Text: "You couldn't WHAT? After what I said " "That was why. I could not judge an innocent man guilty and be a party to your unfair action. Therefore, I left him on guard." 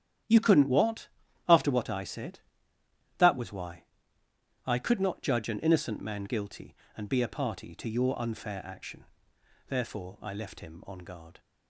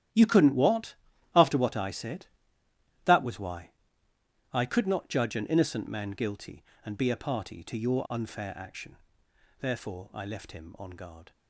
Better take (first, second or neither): first